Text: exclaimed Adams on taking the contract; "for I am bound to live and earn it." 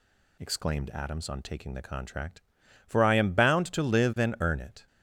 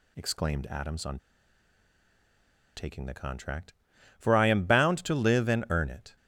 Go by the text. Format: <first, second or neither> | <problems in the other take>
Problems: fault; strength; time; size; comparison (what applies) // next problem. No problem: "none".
first | pauses between "on" and "taking"; strong; at 1.1 s; 1.5 s long